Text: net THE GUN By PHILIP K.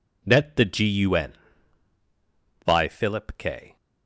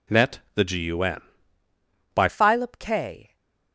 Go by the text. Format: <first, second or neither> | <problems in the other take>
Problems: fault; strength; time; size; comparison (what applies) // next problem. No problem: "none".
first | pauses between "net" and "THE"; slight; at 0.3 s; 0.16 s long // changes voice at "PHILIP"; from 2.2 s on; 1.1 s long